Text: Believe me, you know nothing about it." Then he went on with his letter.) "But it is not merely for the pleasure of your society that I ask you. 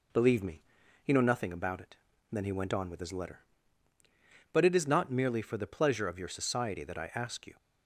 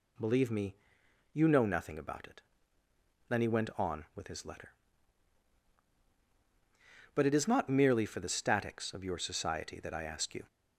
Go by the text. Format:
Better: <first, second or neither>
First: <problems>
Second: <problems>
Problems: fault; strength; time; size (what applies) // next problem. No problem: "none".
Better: first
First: none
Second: says "statics" for "pleasure"; at 8.2 s